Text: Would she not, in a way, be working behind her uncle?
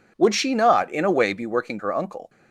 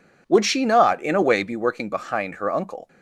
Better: second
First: skips "behind"; at 1.7 s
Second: none

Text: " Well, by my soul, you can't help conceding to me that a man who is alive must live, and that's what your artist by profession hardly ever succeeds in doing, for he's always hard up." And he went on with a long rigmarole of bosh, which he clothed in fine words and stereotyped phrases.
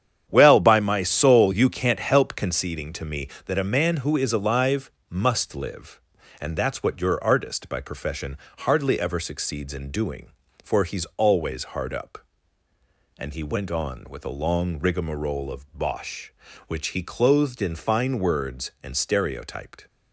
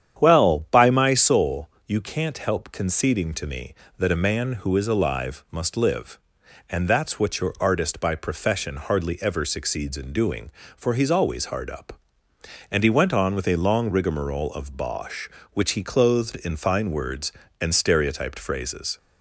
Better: second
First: starts louder than the rest; strong; until 1.2 s; 9 dB // pauses between "alive" and "must"; slight; at 4.8 s; 0.18 s long // pauses between "profession" and "hardly"; slight; at 8.3 s; 0.30 s long // stops before "phrases"; at 19.8 s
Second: starts louder than the rest; strong; until 1.2 s; 9 dB

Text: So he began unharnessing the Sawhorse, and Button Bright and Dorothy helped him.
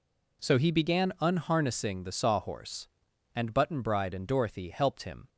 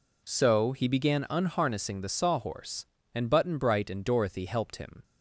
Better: second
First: says "Bride" for "Bright"; at 3.8 s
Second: none

